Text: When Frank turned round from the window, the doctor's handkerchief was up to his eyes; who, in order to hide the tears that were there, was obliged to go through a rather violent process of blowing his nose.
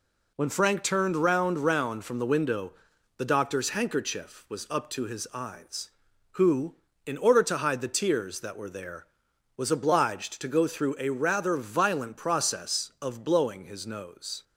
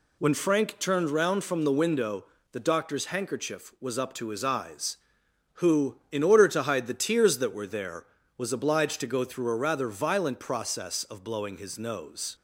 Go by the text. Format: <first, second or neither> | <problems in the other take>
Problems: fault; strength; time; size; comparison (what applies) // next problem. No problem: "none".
second | says "round" twice; at 1.5 s